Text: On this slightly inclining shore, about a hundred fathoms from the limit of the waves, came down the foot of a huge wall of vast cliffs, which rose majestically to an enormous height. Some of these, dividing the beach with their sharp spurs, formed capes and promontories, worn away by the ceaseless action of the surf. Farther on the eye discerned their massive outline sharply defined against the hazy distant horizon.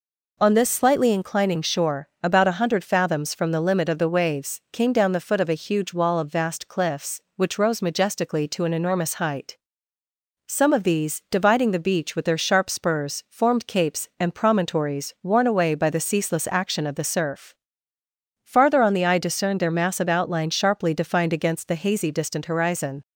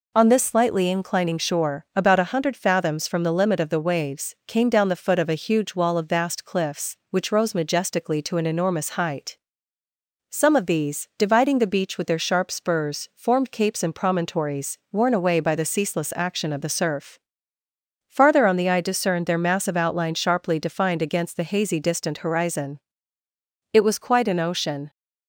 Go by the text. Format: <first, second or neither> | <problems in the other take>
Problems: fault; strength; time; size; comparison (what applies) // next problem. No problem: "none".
first | goes on to say "It was quite an ocean"; noticeable; from 23.7 s on; 1.1 s long